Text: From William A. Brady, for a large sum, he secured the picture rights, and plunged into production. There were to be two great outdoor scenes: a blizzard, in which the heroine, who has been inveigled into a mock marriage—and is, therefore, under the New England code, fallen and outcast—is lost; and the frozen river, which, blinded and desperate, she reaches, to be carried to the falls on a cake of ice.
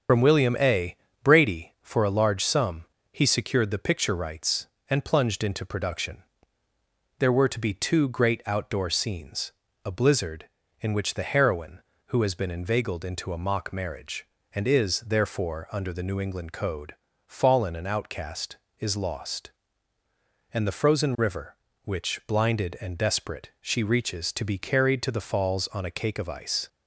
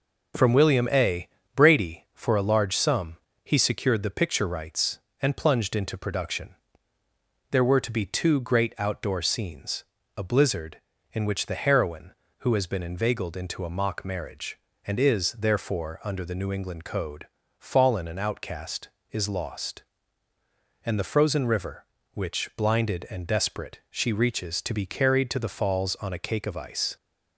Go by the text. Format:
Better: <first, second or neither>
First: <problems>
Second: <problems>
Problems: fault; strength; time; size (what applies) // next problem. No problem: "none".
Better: second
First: loses the start of "From"; at 0.0 s; 75 ms // starts louder than the rest; until 1.3 s; 7 dB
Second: none